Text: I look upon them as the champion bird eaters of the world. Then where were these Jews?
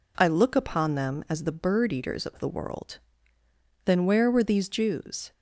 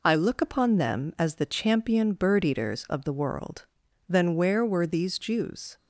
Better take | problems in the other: second | skips "champion"; at 1.5 s

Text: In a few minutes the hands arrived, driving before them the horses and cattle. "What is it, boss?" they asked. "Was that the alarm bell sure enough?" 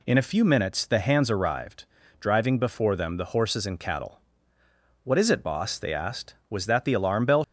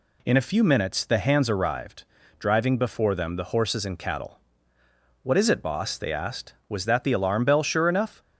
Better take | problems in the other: second | stops before "sure enough"; at 7.4 s

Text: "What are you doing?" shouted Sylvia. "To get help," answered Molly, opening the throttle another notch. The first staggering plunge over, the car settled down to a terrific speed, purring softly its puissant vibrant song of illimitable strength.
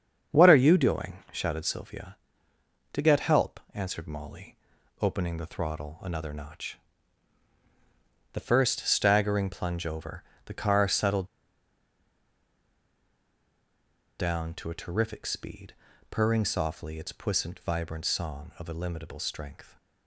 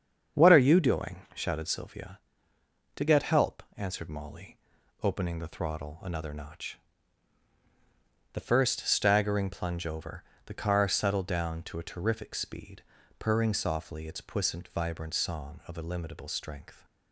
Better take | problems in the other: second | starts louder than the rest; strong; until 1.4 s; 7.5 dB; strong in the second // pauses between "settled" and "down"; strong; at 11.2 s; 2.9 s long

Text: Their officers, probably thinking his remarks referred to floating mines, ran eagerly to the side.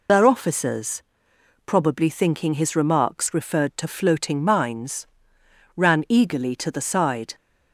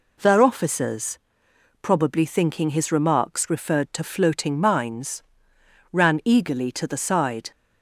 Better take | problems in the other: second | loses the start of "Their"; at 0.0 s; 60 ms

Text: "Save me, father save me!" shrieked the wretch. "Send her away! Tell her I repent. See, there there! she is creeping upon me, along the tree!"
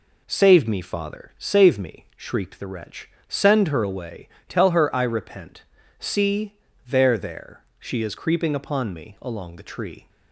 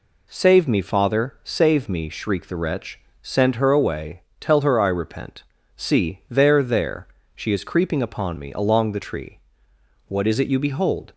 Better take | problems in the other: first | goes on to say "What is it you behold"; noticeable; from 10.0 s on; 1.0 s long

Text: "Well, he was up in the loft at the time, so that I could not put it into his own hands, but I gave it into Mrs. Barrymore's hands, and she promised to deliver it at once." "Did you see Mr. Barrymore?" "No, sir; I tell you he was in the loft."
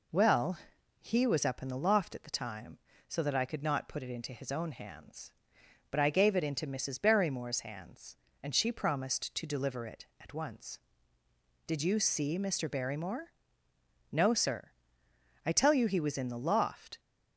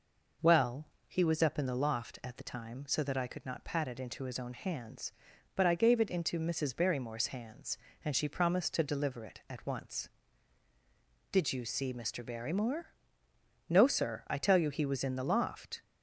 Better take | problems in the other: first | says "pat" for "put"; at 3.6 s

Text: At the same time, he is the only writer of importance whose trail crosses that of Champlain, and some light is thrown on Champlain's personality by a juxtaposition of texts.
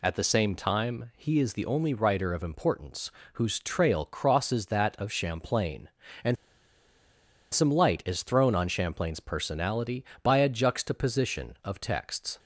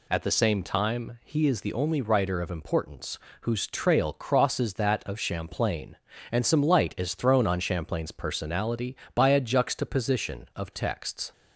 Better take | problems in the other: second | pauses between "importance" and "whose"; slight; at 3.1 s; 0.24 s long; slight in the second // pauses between "and" and "some"; at 6.3 s; 1.1 s long

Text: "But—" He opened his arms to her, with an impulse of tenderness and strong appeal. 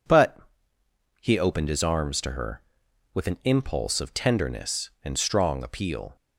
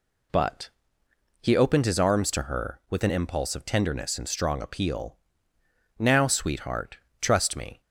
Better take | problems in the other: first | goes on to say "Now sweetheart trust me"; strong; from 5.9 s on; 1.8 s long

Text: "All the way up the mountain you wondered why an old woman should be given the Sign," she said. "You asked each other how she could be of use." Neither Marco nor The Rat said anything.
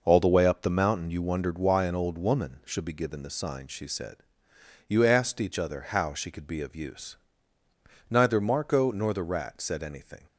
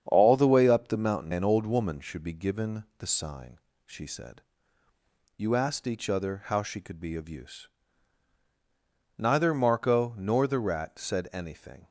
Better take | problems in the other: first | starts louder than the rest; strong; until 1.0 s; 8 dB // skips "you wondered why"; at 1.3 s

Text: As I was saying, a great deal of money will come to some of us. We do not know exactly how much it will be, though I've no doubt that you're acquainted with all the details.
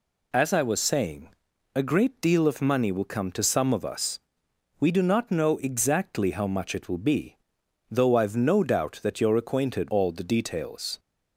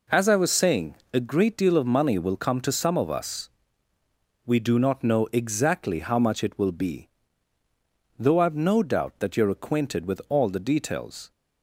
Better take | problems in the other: second | skips "with"; at 9.8 s

